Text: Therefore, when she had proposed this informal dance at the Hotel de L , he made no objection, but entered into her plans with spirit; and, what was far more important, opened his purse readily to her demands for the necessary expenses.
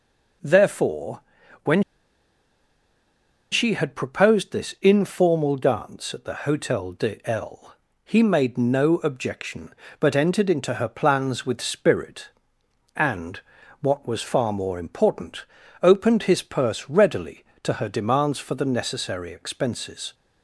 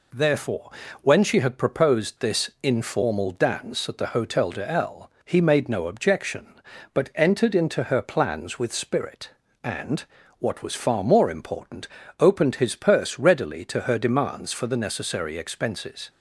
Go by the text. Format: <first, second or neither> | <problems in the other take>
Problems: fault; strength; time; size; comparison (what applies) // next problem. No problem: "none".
second | pauses between "when" and "she"; strong; at 1.8 s; 1.7 s long